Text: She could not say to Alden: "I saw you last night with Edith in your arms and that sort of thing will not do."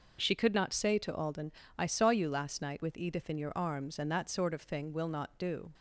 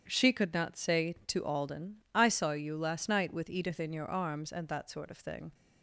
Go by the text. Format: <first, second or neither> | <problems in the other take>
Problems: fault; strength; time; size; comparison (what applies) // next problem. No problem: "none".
first | starts louder than the rest; strong; until 1.0 s; 8.5 dB // stops before "will not do"; at 5.5 s